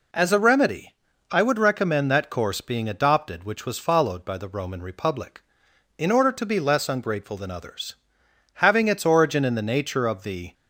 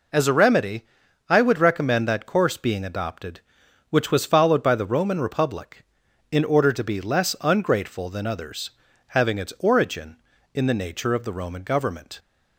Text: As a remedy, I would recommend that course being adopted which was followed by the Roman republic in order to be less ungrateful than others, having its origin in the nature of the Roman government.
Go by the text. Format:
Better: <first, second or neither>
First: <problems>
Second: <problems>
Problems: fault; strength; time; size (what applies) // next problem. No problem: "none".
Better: second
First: stops before "Roman government"; at 10.5 s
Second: none